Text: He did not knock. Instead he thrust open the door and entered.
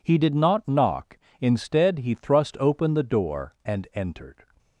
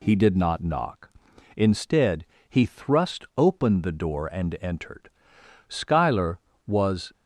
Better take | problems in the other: first | pauses between "Instead" and "he"; slight; at 2.2 s; 0.24 s long // goes on to say "Schuyler was"; from 5.6 s on; 1.4 s long

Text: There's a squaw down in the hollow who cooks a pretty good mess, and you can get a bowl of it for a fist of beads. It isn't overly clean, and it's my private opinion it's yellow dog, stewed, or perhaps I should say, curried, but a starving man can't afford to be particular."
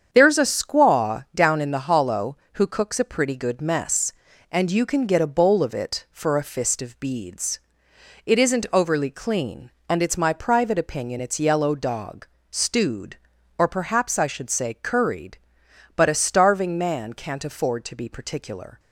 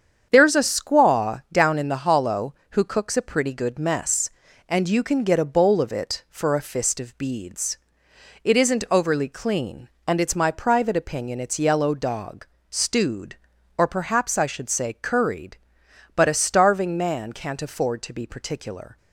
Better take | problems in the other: neither | starts louder than the rest; strong; the same in both

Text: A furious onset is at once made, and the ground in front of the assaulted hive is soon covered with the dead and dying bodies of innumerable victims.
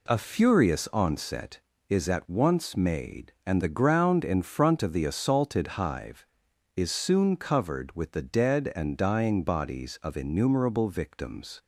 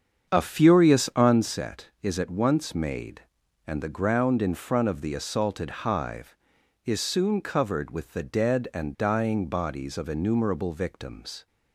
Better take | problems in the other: first | starts louder than the rest; strong; until 1.5 s; 7.5 dB

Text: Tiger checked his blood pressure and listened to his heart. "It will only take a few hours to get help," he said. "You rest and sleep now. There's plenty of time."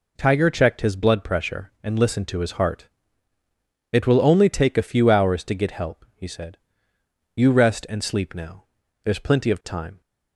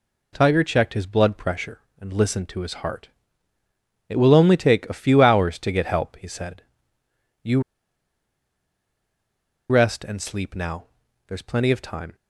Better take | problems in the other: first | pauses between "You" and "rest"; strong; at 7.6 s; 2.0 s long

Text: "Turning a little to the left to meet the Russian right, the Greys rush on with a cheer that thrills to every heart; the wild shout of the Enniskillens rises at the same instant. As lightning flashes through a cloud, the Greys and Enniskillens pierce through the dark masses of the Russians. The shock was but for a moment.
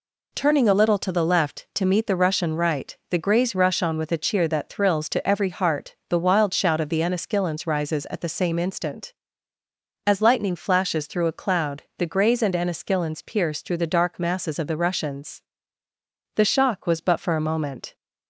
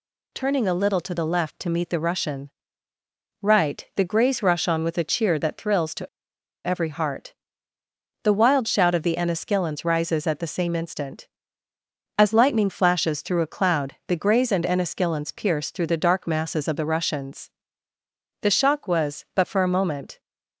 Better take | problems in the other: first | pauses between "Russian" and "right"; noticeable; at 2.5 s; 0.90 s long // pauses between "to" and "every"; noticeable; at 6.0 s; 0.57 s long

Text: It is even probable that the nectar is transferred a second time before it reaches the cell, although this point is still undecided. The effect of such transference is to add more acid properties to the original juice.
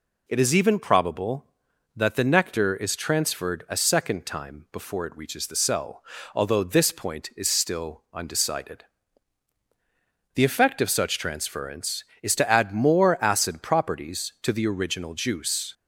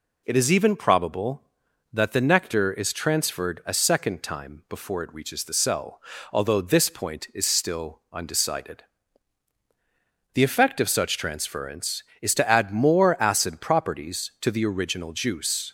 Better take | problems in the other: neither | none

